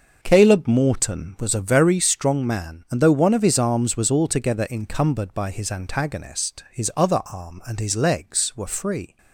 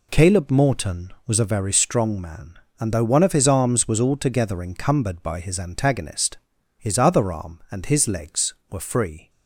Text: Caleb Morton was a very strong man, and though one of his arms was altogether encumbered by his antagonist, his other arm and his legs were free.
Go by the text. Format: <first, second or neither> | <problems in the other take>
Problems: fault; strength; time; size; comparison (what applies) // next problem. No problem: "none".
second | starts louder than the rest; noticeable; until 1.9 s; 6 dB